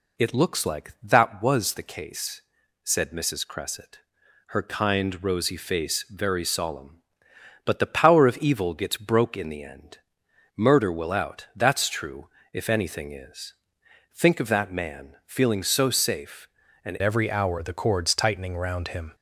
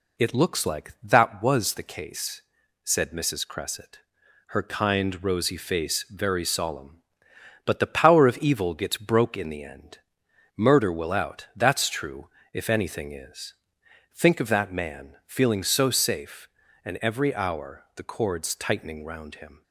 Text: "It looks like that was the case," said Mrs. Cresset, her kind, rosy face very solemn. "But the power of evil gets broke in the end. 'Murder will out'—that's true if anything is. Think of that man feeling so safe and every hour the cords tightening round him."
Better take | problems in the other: second | pauses between "true" and "if"; slight; at 12.2 s; 0.24 s long; slight in the second // changes voice at "every"; from 17.0 s on; 2.1 s long

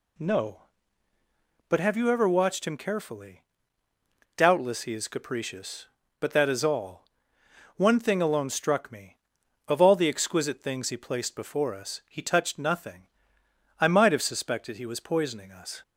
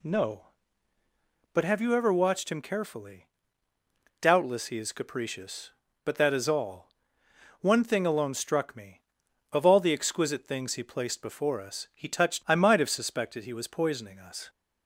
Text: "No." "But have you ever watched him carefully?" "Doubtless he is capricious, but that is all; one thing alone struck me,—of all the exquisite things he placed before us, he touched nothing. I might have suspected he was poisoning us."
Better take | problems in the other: first | skips "nothing"; at 12.4 s

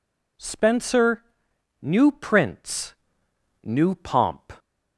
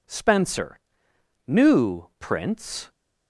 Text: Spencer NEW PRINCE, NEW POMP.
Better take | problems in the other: first | pauses between "Spencer" and "NEW"; noticeable; at 0.7 s; 0.70 s long; noticeable in the first // stops before "NEW POMP"; at 2.9 s

